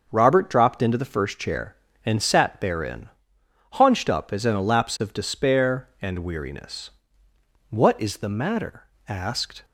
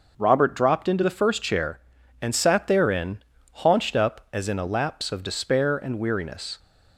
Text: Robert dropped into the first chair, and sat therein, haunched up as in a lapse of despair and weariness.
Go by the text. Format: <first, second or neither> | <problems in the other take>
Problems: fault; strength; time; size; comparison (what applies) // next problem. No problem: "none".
second | starts louder than the rest; until 1.1 s; 6.5 dB // goes on to say "What is the matter asked"; strong; from 7.6 s on; 1.9 s long